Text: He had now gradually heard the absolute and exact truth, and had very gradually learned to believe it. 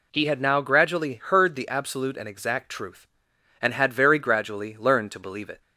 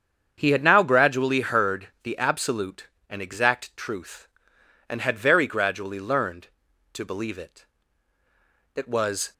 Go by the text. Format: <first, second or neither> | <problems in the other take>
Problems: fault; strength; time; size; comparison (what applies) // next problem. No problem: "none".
first | starts louder than the rest; strong; until 1.3 s; 7.5 dB // goes on to say "It was"; from 8.7 s on; 0.56 s long